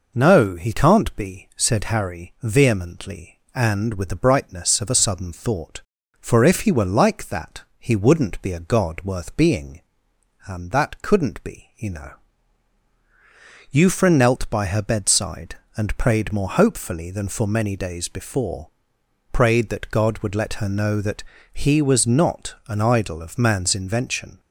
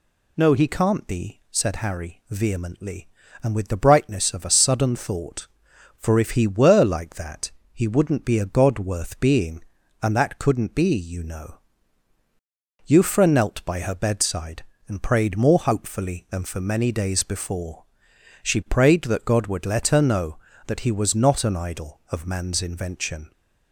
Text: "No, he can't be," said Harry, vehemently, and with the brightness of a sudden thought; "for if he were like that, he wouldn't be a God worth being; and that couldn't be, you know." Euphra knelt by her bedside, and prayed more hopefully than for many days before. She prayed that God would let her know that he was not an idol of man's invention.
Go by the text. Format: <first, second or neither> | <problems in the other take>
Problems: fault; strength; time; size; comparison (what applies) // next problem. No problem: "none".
second | skips "She"; at 19.0 s // pauses between "that" and "he"; slight; at 21.2 s; 0.32 s long